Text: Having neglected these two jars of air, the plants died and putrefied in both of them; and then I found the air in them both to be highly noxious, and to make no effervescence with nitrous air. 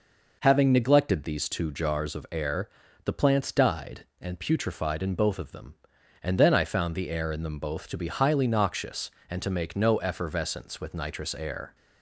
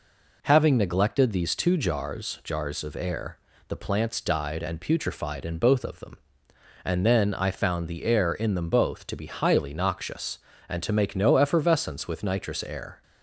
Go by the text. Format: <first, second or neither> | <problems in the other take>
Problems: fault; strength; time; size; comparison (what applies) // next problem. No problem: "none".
first | says "jars" twice; at 2.4 s